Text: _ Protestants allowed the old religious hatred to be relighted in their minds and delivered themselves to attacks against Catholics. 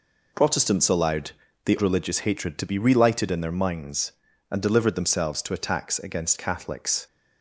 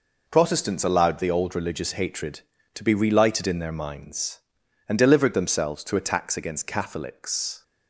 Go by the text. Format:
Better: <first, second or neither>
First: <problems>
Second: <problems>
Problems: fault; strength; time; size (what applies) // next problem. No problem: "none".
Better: second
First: pauses between "allowed" and "the"; slight; at 1.2 s; 0.36 s long // skips "old"; at 1.7 s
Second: none